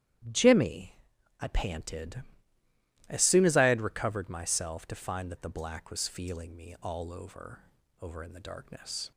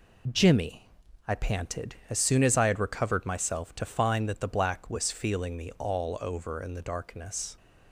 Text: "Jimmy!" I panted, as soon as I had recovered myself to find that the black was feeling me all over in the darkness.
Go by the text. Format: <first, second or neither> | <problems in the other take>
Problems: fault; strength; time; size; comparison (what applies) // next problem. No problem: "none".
second | starts louder than the rest; strong; until 1.7 s; 12 dB // says "over" twice; at 8.0 s